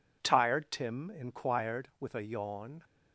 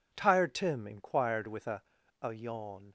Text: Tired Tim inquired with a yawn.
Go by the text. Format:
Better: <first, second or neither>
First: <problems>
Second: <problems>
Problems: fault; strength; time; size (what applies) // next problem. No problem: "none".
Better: first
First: none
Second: says "a" twice; at 2.1 s